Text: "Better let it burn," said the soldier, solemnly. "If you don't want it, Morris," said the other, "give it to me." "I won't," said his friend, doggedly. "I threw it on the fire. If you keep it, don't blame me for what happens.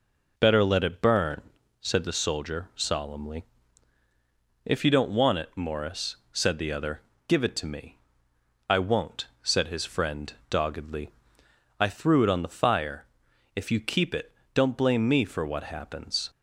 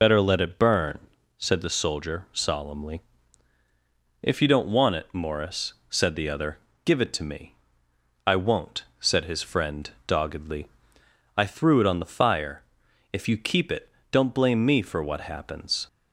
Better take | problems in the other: first | loses the start of "Better"; at 0.0 s; 60 ms

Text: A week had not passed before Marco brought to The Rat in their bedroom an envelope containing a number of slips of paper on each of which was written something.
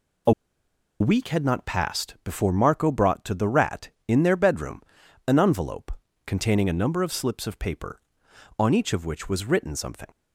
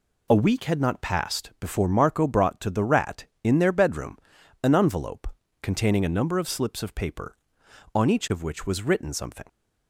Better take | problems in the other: second | pauses between "A" and "week"; noticeable; at 0.3 s; 0.69 s long // pauses between "bedroom" and "an"; at 4.8 s; 0.44 s long; also in the second // pauses between "envelope" and "containing"; slight; at 5.9 s; 0.36 s long; slight in the second

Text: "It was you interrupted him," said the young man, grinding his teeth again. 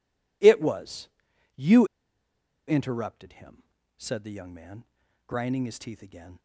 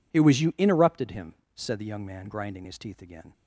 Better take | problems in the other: second | pauses between "was" and "you"; noticeable; at 1.0 s; 0.46 s long // pauses between "you" and "interrupted"; noticeable; at 1.8 s; 0.81 s long

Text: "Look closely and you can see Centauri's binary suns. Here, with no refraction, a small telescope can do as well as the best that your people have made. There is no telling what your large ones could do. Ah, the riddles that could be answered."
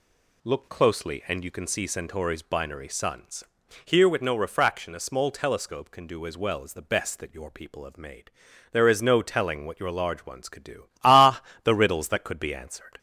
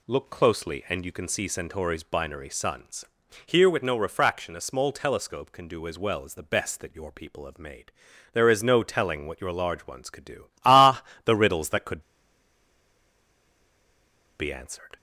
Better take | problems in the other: first | pauses between "could" and "be"; strong; at 12.0 s; 2.3 s long

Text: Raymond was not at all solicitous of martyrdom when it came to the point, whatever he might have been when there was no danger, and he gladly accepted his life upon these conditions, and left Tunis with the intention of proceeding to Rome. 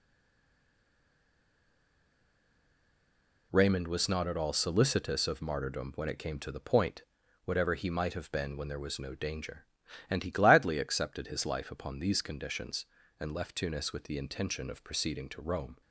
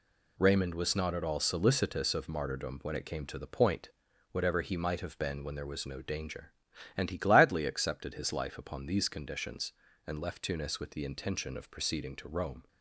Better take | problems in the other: second | stays silent before the first word; strong; until 3.5 s; 3.5 s long

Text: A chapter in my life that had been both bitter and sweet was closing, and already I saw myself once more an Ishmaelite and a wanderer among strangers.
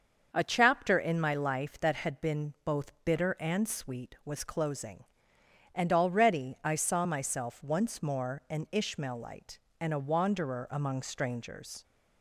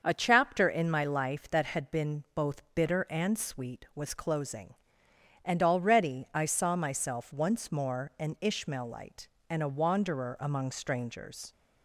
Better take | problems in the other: neither | starts louder than the rest; the same in both

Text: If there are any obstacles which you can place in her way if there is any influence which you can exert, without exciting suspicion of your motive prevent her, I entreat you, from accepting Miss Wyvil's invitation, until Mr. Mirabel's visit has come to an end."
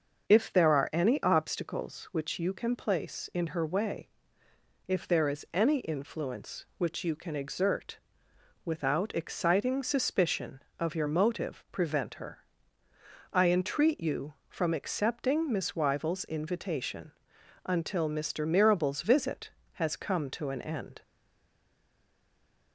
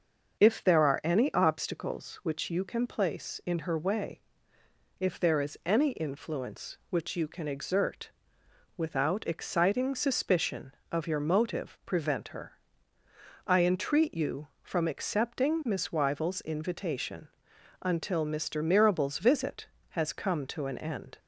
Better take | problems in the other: second | starts louder than the rest; until 1.3 s; 6 dB; also in the second // pauses between "way" and "if"; noticeable; at 4.0 s; 0.80 s long; noticeable in the second // stays silent after the last word; noticeable; from 21.0 s on; 1.7 s long

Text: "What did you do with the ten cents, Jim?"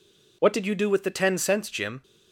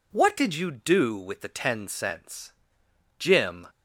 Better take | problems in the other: neither | none

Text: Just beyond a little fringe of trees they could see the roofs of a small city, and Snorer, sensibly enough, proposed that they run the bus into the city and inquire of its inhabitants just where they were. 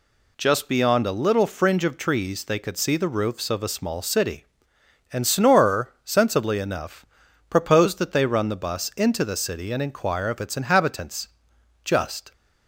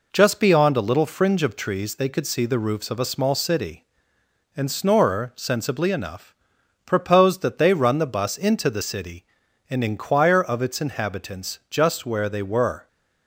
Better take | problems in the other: second | pauses between "inhabitants" and "just"; noticeable; at 11.2 s; 0.56 s long // stops before "where they were"; at 12.3 s

